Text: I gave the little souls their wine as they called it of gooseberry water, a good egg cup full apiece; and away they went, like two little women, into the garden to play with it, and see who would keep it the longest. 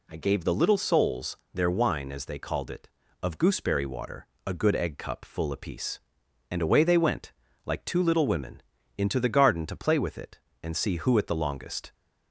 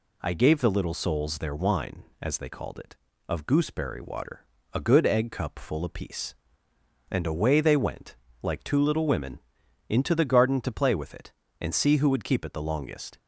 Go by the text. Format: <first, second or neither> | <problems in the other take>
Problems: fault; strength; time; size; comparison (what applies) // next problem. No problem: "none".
second | pauses between "souls" and "their"; slight; at 1.3 s; 0.16 s long // skips "would keep"; at 11.1 s